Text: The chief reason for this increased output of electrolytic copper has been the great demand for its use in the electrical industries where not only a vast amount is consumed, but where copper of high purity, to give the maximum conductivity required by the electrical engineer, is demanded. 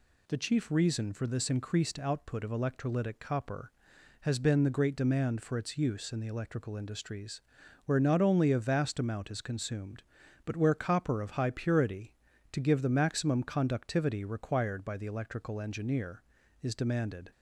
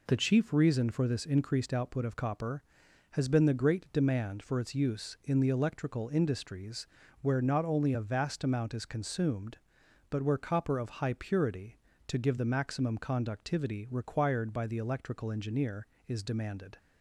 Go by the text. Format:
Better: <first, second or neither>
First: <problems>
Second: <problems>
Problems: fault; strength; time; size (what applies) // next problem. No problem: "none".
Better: first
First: pauses between "industries" and "where"; at 7.4 s; 0.44 s long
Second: skips "electrolytic"; at 2.1 s // pauses between "industries" and "where"; slight; at 6.8 s; 0.36 s long